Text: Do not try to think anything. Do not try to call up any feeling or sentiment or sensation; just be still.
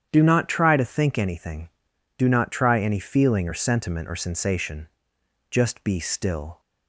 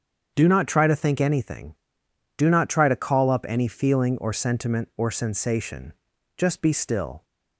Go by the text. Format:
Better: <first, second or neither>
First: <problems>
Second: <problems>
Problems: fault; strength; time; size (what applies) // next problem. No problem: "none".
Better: second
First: starts louder than the rest; strong; until 1.1 s; 9 dB // skips "to call up"; at 2.8 s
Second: starts louder than the rest; strong; until 1.3 s; 7.5 dB